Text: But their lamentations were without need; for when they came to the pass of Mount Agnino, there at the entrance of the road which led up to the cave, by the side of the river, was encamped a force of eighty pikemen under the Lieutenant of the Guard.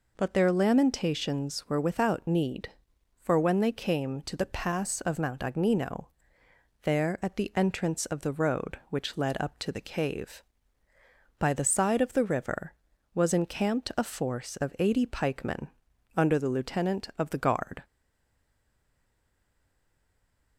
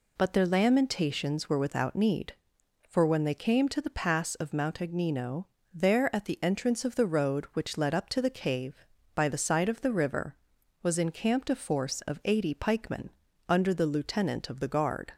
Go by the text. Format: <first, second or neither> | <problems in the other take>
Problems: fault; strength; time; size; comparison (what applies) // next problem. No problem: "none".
second | pauses between "pikemen" and "under"; noticeable; at 15.6 s; 0.48 s long; also in the second // stays silent after the last word; strong; from 17.8 s on; 2.7 s long